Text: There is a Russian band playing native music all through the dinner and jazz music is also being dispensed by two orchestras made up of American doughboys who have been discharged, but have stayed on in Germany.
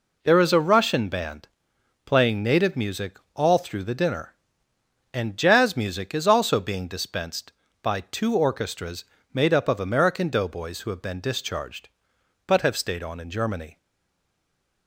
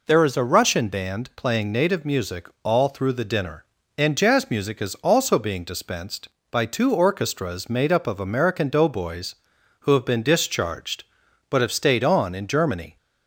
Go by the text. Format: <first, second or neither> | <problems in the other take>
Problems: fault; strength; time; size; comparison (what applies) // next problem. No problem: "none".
second | pauses between "band" and "playing"; noticeable; at 1.4 s; 0.56 s long // pauses between "music" and "all"; slight; at 3.1 s; 0.18 s long; slight in the second // pauses between "orchestras" and "made"; slight; at 9.0 s; 0.28 s long // stays silent after the last word; from 13.7 s on; 1.1 s long